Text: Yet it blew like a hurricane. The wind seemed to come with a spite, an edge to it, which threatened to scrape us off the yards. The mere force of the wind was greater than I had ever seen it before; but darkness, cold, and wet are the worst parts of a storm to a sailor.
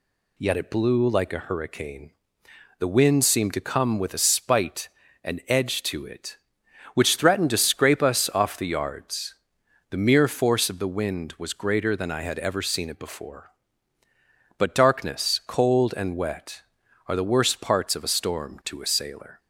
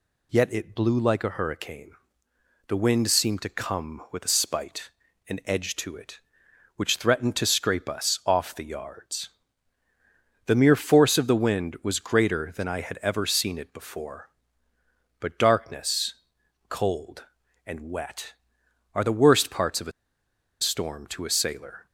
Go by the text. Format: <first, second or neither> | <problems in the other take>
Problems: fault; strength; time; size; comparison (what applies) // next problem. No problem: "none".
first | pauses between "a" and "storm"; noticeable; at 19.9 s; 0.70 s long